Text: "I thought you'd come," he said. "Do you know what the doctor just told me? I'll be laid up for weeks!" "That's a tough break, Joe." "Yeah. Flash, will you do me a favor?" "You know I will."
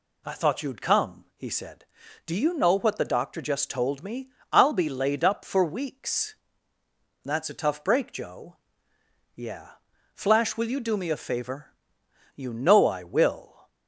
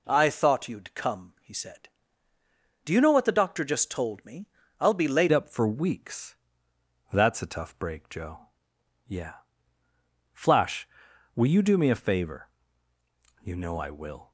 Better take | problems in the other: first | changes voice at "up"; from 5.3 s on; 9.0 s long

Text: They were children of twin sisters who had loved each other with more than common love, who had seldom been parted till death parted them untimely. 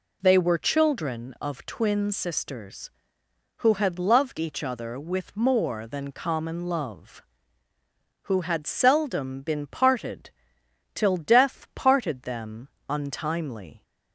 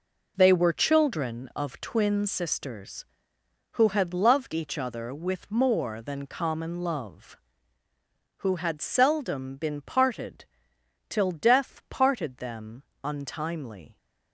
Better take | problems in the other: first | gets quieter; strong; throughout; 8 dB // pauses between "parted" and "till"; noticeable; at 10.4 s; 0.64 s long; noticeable in the first // pauses between "them" and "untimely"; slight; at 12.8 s; 0.20 s long; slight in the first

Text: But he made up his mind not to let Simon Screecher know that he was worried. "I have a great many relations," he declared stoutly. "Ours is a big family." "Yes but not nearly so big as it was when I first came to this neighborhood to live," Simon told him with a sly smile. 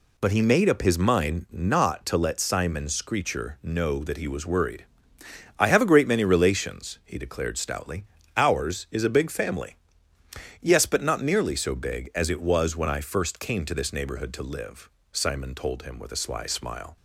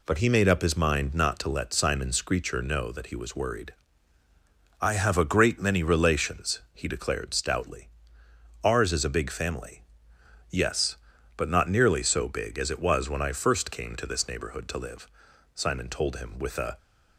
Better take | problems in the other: first | stops before "sly smile"; at 16.7 s

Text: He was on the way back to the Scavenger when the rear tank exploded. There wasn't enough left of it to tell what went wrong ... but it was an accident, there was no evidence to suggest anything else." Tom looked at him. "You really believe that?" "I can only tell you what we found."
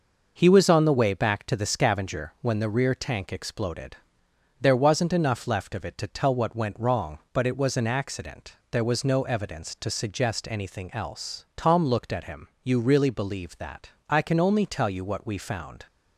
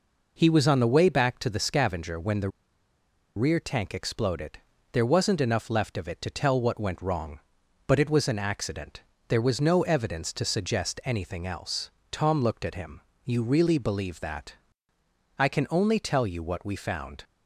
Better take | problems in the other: first | pauses between "the" and "rear"; noticeable; at 2.4 s; 0.87 s long

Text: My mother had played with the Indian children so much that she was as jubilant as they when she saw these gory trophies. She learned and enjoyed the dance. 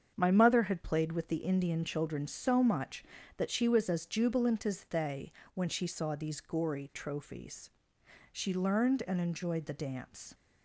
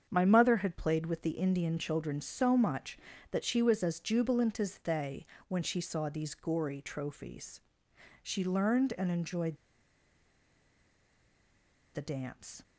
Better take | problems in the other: first | starts louder than the rest; strong; until 1.1 s; 7.5 dB; strong in the first // pauses between "they" and "when"; slight; at 5.2 s; 0.24 s long; slight in the first // pauses between "enjoyed" and "the"; strong; at 9.5 s; 2.3 s long

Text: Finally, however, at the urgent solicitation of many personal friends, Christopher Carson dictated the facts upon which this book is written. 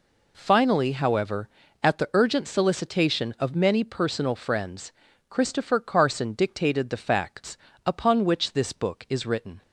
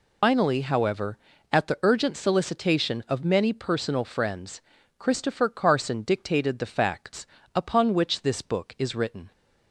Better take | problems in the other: first | loses the start of "Finally"; at 0.2 s; 180 ms // pauses between "facts" and "upon"; slight; at 7.2 s; 0.30 s long; slight in the first

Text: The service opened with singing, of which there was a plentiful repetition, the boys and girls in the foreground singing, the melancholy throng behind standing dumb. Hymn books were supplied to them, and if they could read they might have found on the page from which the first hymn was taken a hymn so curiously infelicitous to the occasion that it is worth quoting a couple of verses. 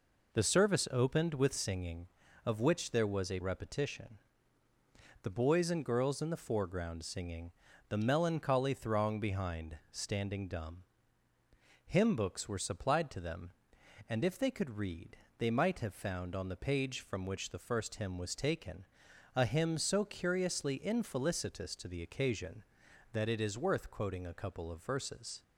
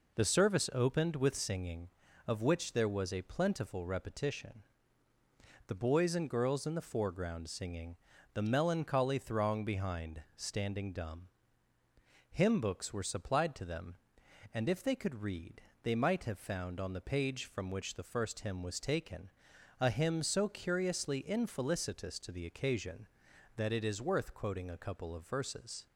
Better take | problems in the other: second | skips "plentiful"; at 3.3 s // pauses between "read" and "they"; slight; at 15.1 s; 0.22 s long; slight in the second // pauses between "taken" and "a"; noticeable; at 18.8 s; 0.50 s long; noticeable in the second

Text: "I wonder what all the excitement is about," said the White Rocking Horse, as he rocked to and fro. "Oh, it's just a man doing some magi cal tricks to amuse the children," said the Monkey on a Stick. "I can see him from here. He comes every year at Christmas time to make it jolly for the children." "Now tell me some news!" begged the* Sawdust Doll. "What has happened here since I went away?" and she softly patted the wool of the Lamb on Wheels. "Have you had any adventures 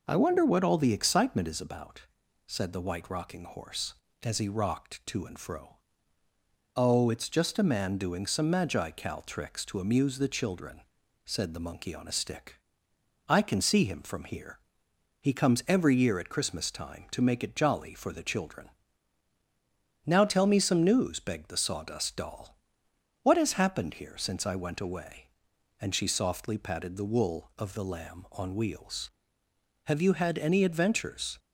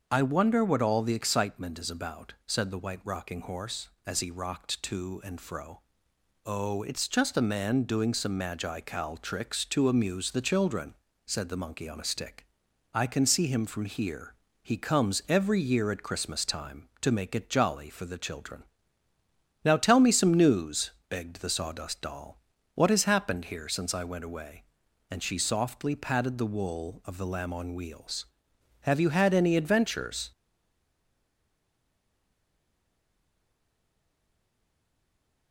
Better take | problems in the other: first | starts louder than the rest; until 1.1 s; 6.5 dB // stays silent after the last word; strong; from 30.3 s on; 5.2 s long

